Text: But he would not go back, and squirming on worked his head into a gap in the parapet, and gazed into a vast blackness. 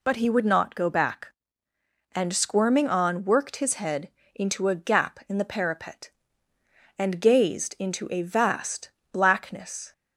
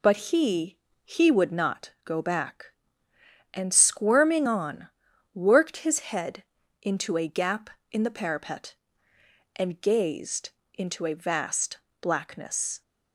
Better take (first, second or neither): first